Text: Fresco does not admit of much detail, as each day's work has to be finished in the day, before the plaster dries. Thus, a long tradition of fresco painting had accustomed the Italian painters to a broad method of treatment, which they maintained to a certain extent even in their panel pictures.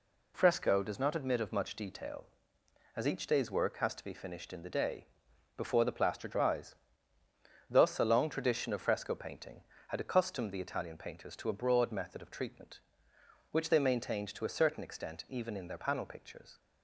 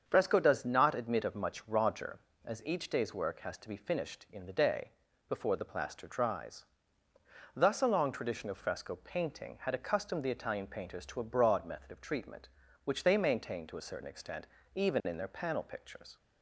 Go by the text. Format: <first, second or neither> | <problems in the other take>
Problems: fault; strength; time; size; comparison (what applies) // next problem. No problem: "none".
first | starts louder than the rest; strong; until 1.0 s; 7 dB // says "roger" for "detail"; at 1.6 s // pauses between "extent" and "even"; slight; at 14.4 s; 0.30 s long